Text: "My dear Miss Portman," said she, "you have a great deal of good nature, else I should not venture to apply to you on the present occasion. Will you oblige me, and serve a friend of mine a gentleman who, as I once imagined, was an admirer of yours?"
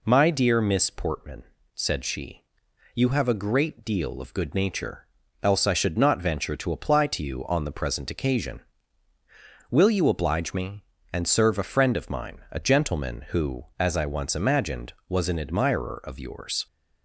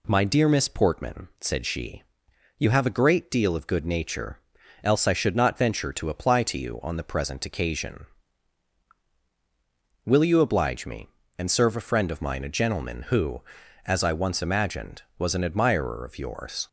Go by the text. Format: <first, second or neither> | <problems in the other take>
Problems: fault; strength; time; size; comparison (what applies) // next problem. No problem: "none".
neither | none